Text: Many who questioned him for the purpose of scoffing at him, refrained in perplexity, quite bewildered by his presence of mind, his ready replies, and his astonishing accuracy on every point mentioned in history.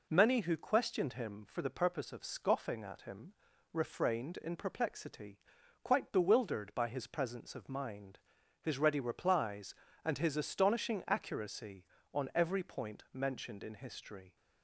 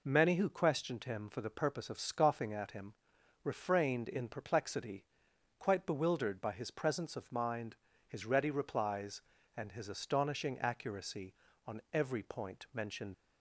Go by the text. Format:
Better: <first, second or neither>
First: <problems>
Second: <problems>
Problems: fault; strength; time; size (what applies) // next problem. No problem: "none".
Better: first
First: none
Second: stops before "in history"; at 13.1 s